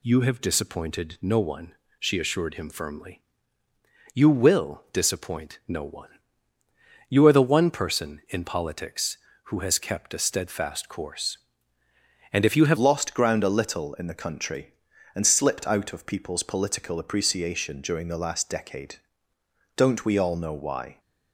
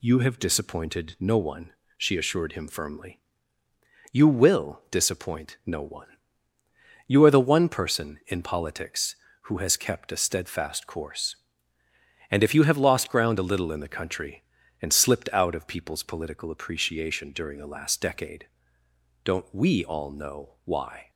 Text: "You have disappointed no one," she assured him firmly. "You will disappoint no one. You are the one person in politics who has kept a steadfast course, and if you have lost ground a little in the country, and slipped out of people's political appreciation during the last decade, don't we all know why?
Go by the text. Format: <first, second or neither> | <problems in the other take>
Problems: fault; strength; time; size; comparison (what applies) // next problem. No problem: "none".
second | changes voice at "lost"; from 12.7 s on; 8.2 s long